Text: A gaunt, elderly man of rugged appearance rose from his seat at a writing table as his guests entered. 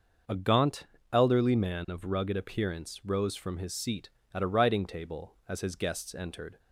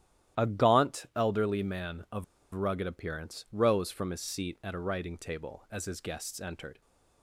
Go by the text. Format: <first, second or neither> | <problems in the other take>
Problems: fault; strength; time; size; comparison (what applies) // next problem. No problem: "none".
first | starts louder than the rest; strong; until 1.4 s; 12.5 dB; also in the first // pauses between "of" and "rugged"; slight; at 2.2 s; 0.30 s long